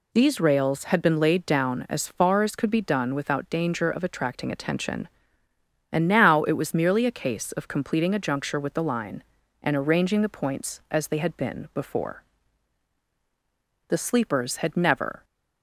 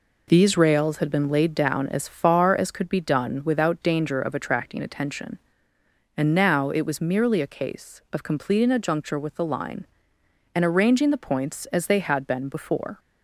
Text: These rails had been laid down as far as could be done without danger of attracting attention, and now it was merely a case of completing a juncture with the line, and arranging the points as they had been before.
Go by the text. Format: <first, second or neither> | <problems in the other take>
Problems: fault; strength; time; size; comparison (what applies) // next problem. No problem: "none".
second | goes on to say "The sleepers had never"; from 13.8 s on; 1.3 s long